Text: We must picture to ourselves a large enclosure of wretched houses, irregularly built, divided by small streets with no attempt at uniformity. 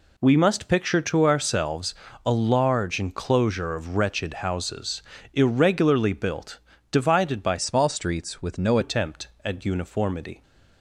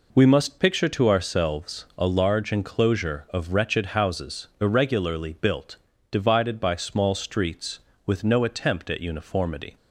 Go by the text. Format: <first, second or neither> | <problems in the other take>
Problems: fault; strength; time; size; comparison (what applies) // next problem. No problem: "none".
second | pauses between "ourselves" and "a"; slight; at 1.9 s; 0.32 s long // changes voice from "small" to "no"; from 7.5 to 8.7 s; 1.2 s long